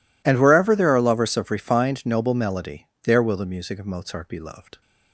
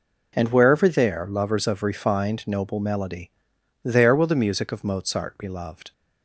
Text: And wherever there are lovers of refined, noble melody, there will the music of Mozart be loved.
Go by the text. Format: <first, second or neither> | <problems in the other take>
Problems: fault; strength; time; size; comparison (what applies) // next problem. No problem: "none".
first | skips "are"; at 1.2 s